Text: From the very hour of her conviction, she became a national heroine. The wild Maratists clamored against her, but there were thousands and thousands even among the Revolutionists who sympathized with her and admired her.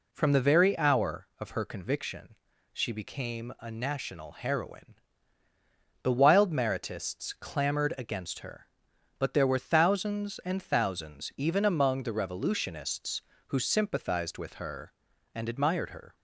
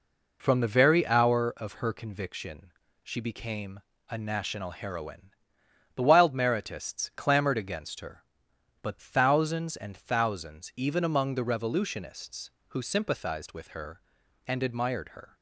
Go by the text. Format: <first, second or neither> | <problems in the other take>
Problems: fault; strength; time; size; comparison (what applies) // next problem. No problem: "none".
first | pauses between "became" and "a"; slight; at 3.7 s; 0.30 s long // skips "there were"; at 8.9 s